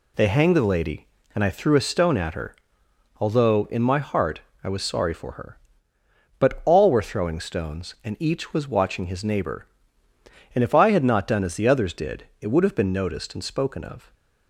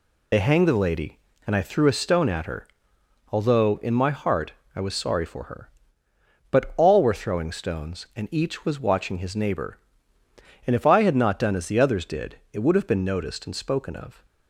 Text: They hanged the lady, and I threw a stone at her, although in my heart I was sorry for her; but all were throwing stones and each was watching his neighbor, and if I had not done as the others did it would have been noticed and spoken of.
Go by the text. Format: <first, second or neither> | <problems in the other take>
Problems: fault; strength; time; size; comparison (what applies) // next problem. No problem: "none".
first | loses the start of "They"; at 0.3 s; 55 ms // pauses between "heart" and "I"; slight; at 4.5 s; 0.22 s long; slight in the first // pauses between "did" and "it"; slight; at 12.3 s; 0.16 s long; slight in the first